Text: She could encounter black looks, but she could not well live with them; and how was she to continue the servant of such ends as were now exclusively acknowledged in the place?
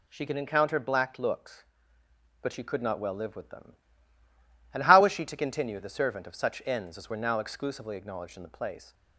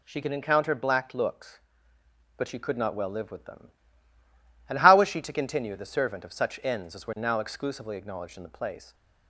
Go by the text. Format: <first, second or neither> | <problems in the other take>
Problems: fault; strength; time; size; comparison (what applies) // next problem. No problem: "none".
neither | none